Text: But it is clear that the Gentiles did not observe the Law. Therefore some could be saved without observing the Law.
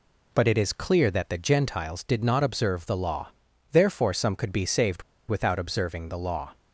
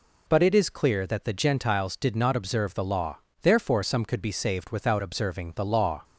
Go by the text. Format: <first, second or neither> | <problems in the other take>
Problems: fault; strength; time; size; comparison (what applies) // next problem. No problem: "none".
second | pauses between "saved" and "without"; slight; at 5.0 s; 0.26 s long